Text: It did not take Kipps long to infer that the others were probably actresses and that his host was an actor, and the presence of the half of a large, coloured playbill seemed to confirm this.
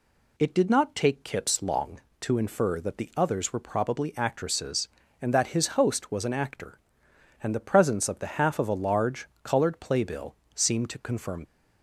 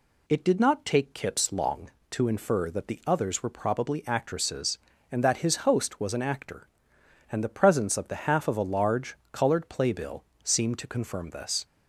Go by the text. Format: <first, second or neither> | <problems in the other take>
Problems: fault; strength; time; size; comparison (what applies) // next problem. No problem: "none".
second | pauses between "playbill" and "seemed"; slight; at 10.3 s; 0.20 s long; slight in the second // stops before "this"; at 11.4 s